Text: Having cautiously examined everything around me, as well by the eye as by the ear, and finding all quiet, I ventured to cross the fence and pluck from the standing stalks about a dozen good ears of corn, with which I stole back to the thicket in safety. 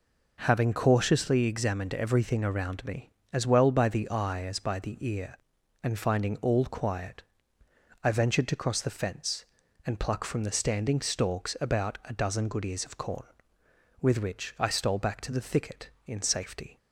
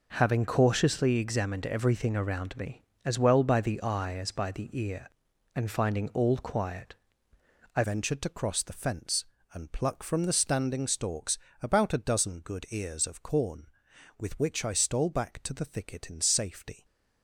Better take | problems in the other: first | changes voice at "ventured"; from 7.8 s on; 9.0 s long // pauses between "stalks" and "about"; slight; at 11.3 s; 0.24 s long

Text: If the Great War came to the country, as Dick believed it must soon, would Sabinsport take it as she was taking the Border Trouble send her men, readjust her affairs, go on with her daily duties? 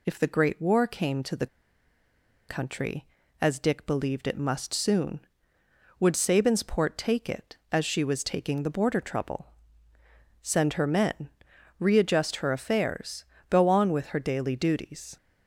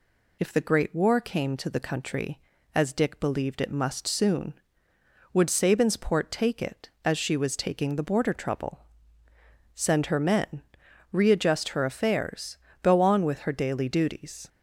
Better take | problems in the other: second | pauses between "the" and "country"; at 1.4 s; 1.0 s long // pauses between "Trouble" and "send"; noticeable; at 9.4 s; 0.96 s long; noticeable in the second

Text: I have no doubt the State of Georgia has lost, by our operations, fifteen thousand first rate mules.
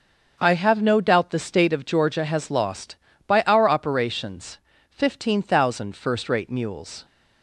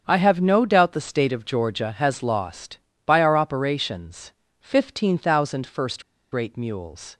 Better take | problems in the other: first | starts louder than the rest; strong; until 1.0 s; 7.5 dB; also in the first // pauses between "first" and "rate"; slight; at 6.0 s; 0.29 s long

